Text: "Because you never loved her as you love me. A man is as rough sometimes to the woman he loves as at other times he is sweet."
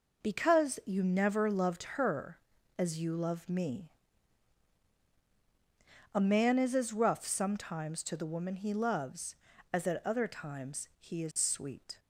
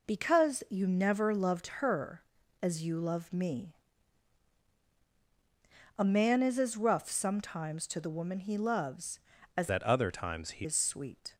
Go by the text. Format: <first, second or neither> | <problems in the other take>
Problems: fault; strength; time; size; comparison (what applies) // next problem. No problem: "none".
first | changes voice from "at" to "he"; from 9.6 to 10.6 s; 1.0 s long